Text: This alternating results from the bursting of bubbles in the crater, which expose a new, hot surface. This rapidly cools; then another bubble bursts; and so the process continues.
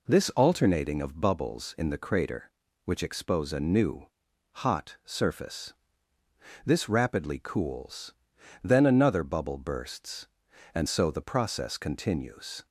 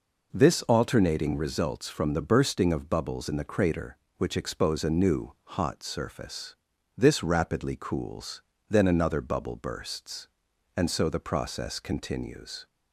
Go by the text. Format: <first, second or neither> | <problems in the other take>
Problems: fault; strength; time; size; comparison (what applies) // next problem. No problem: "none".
second | skips "results from the bursting"; at 1.0 s